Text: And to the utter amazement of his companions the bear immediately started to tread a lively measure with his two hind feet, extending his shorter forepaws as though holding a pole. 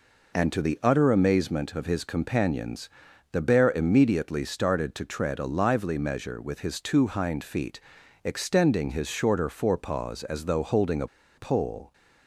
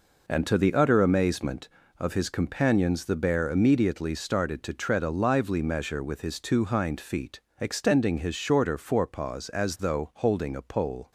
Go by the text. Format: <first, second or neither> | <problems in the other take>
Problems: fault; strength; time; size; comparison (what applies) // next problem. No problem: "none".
second | pauses between "companions" and "the"; at 2.8 s; 0.44 s long // pauses between "a" and "pole"; slight; at 11.0 s; 0.30 s long